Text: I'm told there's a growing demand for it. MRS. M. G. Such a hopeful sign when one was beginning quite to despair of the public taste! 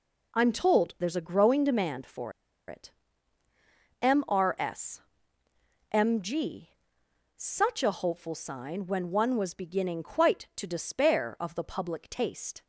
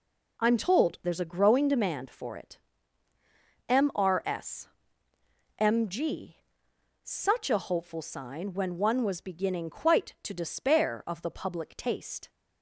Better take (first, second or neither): second